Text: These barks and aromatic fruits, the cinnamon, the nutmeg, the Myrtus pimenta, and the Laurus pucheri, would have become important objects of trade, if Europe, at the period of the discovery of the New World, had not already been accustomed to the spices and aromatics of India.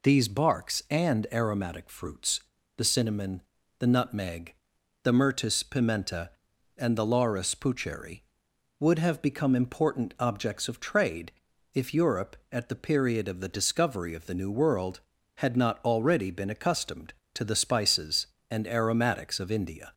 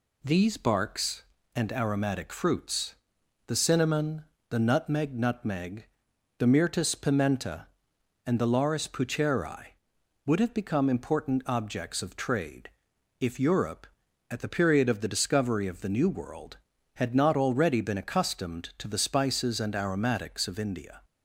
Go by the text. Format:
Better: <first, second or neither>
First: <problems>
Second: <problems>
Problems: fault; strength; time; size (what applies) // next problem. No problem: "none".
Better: first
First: none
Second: says "nutmeg" twice; at 5.1 s